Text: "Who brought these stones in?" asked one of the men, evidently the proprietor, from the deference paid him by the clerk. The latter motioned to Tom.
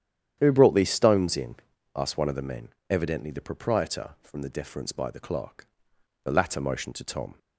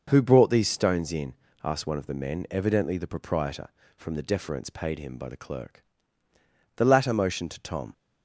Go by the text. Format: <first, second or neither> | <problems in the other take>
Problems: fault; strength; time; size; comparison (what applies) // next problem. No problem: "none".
second | starts louder than the rest; strong; until 1.4 s; 9.5 dB // skips "paid him"; at 4.9 s